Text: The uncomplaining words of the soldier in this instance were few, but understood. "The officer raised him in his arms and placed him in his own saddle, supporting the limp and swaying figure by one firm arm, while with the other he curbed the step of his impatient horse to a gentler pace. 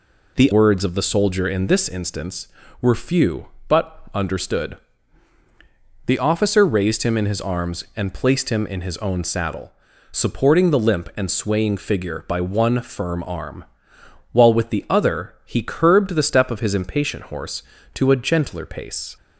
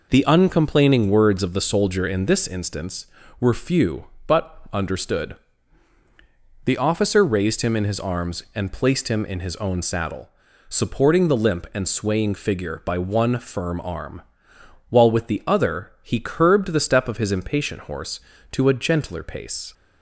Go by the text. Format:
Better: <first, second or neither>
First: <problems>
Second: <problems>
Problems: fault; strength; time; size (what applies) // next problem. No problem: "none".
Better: second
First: skips "uncomplaining"; at 0.5 s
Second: none